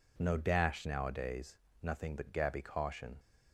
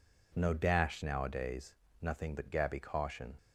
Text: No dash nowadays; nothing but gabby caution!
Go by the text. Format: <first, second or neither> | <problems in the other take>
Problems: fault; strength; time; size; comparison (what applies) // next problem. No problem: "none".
neither | none